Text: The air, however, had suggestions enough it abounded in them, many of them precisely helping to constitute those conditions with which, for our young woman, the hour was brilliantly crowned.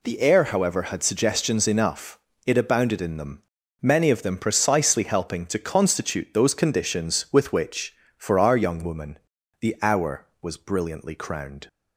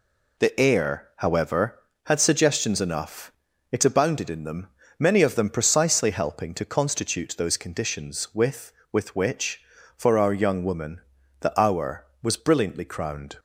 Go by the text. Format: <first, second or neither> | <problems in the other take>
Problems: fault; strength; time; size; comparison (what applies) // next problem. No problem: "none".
first | pauses between "enough" and "it"; at 3.3 s; 0.40 s long; slight in the first // says "with" twice; at 8.9 s